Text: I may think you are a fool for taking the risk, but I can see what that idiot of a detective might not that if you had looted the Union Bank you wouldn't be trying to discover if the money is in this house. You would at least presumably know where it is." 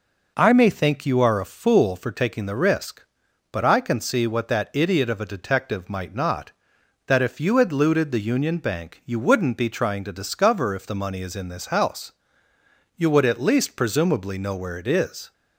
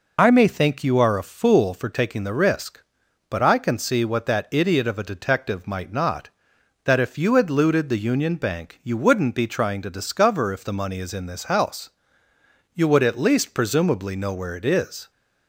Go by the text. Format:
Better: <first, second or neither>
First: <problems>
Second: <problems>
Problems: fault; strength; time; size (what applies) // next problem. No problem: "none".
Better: first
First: none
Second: loses the start of "I"; at 0.1 s; 45 ms